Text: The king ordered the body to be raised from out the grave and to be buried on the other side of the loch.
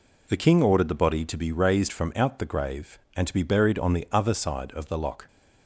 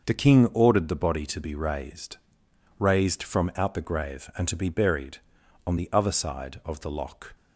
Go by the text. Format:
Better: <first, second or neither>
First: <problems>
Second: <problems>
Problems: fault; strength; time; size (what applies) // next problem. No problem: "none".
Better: first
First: none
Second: starts louder than the rest; until 1.0 s; 6 dB // says "raised" twice; at 2.7 s